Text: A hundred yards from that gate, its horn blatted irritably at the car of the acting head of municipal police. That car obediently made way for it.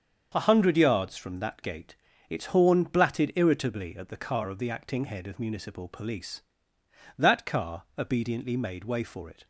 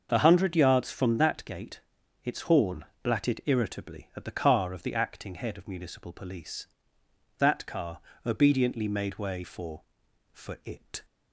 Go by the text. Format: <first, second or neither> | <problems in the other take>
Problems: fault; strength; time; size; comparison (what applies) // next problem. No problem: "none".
first | starts louder than the rest; until 1.1 s; 6.5 dB; also in the first // pauses between "horn" and "blatted"; slight; at 2.8 s; 0.20 s long // pauses between "car" and "obediently"; slight; at 7.9 s; 0.26 s long // says "for" twice; at 10.3 s